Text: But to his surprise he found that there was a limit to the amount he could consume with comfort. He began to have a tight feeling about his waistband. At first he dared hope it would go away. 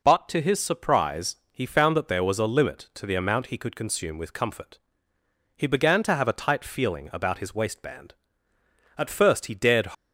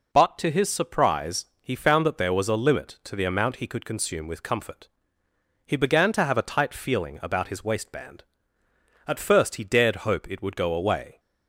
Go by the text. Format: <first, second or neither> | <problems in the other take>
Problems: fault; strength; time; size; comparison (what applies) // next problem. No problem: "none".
second | pauses between "surprise" and "he"; slight; at 1.3 s; 0.16 s long; slight in the second // stops before "hope it would go away"; at 9.9 s